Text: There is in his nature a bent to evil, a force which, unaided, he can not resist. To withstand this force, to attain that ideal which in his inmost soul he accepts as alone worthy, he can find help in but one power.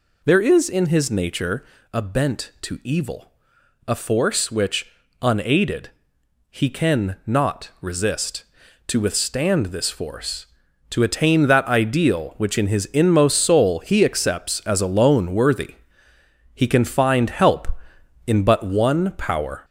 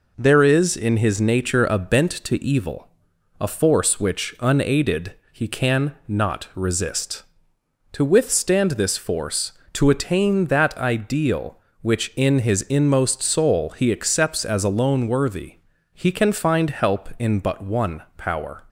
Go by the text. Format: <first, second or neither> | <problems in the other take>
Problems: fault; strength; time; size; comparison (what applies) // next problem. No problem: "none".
second | gets louder; noticeable; throughout; 4 dB // pauses between "nature" and "a"; slight; at 1.6 s; 0.28 s long